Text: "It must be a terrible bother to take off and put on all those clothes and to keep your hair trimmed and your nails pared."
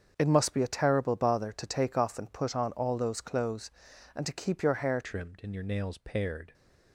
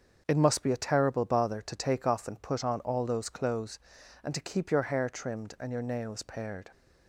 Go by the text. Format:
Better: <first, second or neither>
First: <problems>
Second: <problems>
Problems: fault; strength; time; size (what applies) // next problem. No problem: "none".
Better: second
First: starts louder than the rest; until 1.1 s; 7 dB // changes voice at "trimmed"; from 5.0 s on; 1.5 s long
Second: starts louder than the rest; until 1.2 s; 7 dB